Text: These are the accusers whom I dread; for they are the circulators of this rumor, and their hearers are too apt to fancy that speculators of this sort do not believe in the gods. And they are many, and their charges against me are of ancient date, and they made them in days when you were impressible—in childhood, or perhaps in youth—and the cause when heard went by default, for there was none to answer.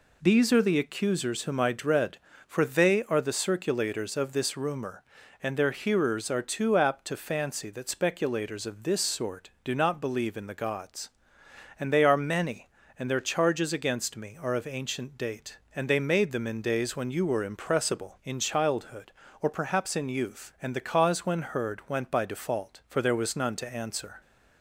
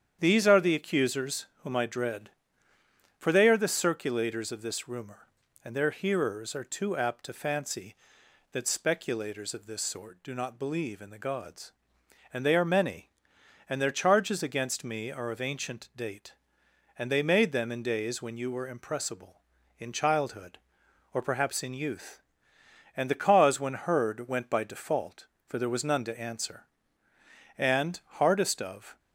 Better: first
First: none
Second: starts louder than the rest; strong; until 1.2 s; 8.5 dB // pauses between "accusers" and "whom"; slight; at 1.4 s; 0.16 s long // goes on to say "And hardest of"; from 27.5 s on; 1.4 s long

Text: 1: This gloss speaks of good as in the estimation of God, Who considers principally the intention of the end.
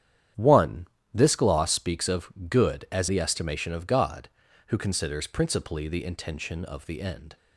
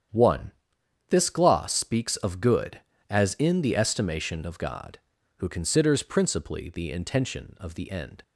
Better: second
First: starts louder than the rest; strong; until 1.6 s; 10 dB // pauses between "of" and "good"; slight; at 2.3 s; 0.16 s long // skips "in"; at 3.0 s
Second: starts louder than the rest; strong; until 1.6 s; 9 dB

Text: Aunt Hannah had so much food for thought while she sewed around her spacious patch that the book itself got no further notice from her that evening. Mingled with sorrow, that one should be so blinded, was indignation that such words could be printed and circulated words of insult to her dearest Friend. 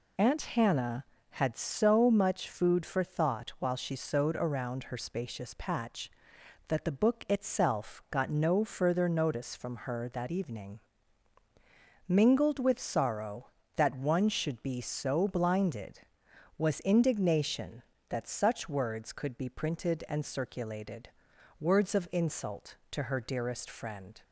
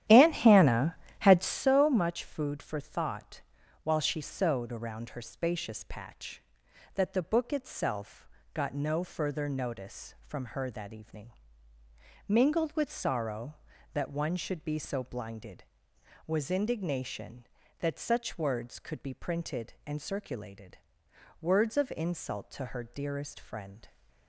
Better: first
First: pauses between "circulated" and "words"; noticeable; at 21.0 s; 0.50 s long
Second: starts louder than the rest; strong; until 1.7 s; 11.5 dB // pauses between "thought" and "while"; at 3.4 s; 0.42 s long // pauses between "itself" and "got"; slight; at 8.2 s; 0.26 s long // pauses between "circulated" and "words"; noticeable; at 20.7 s; 0.64 s long

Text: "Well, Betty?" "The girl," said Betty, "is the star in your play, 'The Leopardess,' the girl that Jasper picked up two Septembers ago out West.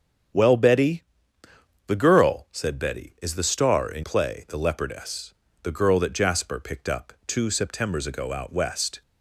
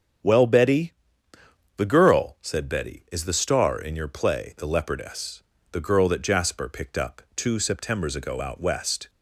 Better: second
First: starts louder than the rest; strong; until 2.1 s; 8 dB // skips "your"; at 4.0 s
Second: starts louder than the rest; strong; until 2.0 s; 7.5 dB

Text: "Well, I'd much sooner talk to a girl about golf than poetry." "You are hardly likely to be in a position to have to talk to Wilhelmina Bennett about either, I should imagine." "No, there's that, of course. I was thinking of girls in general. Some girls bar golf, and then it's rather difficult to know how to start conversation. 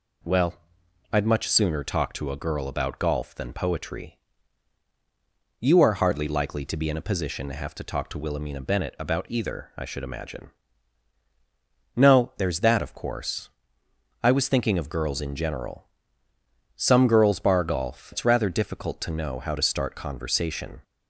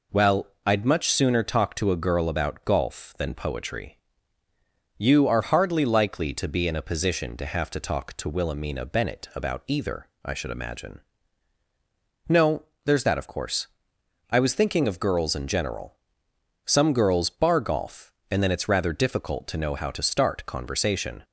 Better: second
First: skips "and then"; at 18.1 s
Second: none

